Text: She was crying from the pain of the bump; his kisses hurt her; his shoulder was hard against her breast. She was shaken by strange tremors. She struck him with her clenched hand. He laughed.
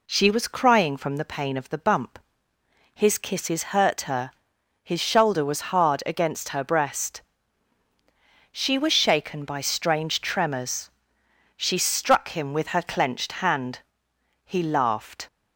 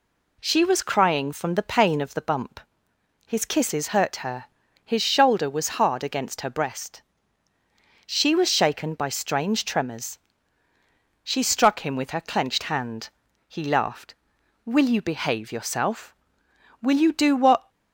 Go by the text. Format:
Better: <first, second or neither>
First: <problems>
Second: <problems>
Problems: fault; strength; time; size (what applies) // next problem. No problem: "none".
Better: first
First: none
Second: goes on to say "Will you behave yourself Will you do what"; strong; from 14.6 s on; 3.0 s long